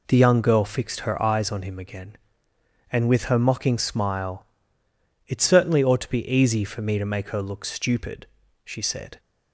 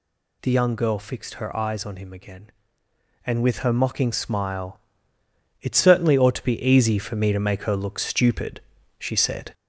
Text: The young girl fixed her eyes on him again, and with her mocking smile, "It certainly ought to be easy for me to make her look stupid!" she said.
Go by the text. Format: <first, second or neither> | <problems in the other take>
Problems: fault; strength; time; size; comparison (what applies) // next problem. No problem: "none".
first | gets louder; slight; throughout; 2.5 dB